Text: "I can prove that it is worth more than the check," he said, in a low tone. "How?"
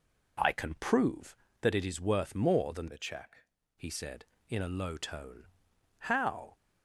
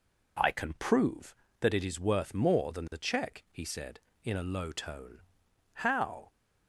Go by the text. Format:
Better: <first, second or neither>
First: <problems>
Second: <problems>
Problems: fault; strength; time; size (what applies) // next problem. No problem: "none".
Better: second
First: changes voice from "the" to "check"; from 2.8 to 3.4 s; 0.6 s long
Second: none